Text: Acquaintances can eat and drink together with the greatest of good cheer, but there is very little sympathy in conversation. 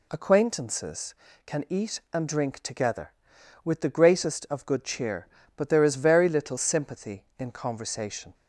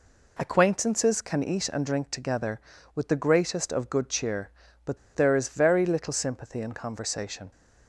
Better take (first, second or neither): first